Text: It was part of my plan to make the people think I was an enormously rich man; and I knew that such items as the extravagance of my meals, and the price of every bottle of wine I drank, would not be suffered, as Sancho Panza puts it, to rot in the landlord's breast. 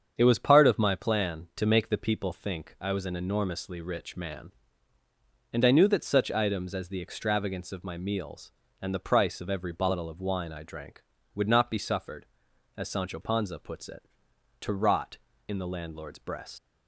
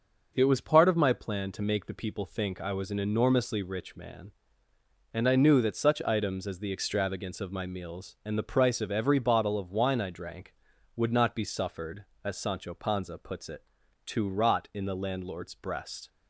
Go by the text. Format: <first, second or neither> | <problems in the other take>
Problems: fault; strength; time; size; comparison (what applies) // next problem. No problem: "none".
second | starts louder than the rest; strong; until 1.1 s; 7.5 dB; also in the second // leaves "breast" unfinished; at 16.5 s; 100 ms